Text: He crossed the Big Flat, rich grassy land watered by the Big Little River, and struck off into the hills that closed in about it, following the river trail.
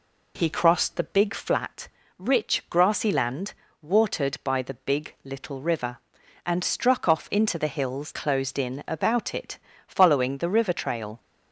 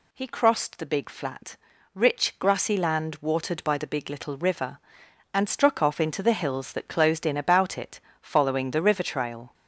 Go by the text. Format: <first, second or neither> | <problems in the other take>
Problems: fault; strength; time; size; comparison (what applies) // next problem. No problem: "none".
second | pauses between "land" and "watered"; slight; at 3.5 s; 0.26 s long // skips "that"; at 8.1 s